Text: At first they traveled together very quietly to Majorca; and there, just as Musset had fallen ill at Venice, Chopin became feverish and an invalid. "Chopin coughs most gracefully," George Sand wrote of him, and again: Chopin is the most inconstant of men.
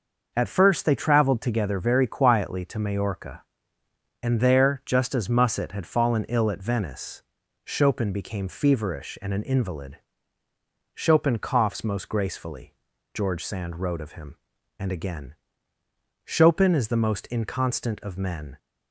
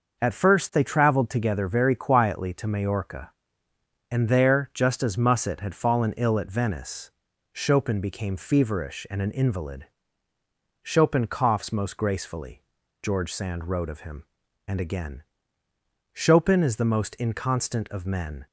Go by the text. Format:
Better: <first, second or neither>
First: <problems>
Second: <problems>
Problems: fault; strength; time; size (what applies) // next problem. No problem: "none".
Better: neither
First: none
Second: none